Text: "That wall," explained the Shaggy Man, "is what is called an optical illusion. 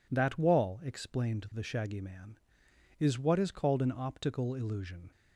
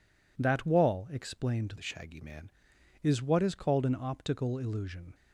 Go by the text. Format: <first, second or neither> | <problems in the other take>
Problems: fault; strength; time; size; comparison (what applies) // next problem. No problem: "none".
first | changes voice from "the" to "Man"; from 1.7 to 2.4 s; 0.7 s long